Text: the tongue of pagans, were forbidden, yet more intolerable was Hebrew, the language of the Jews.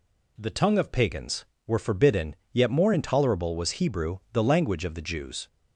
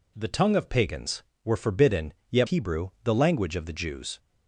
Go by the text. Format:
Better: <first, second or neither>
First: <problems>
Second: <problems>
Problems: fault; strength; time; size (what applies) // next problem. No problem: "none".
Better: first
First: none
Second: skips "more intolerable was"; at 2.4 s